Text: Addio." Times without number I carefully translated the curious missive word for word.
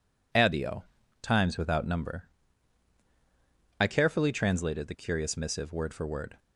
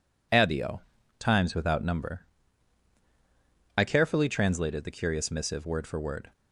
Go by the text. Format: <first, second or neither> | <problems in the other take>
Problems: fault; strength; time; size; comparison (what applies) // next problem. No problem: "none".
neither | pauses between "number" and "I"; strong; the same in both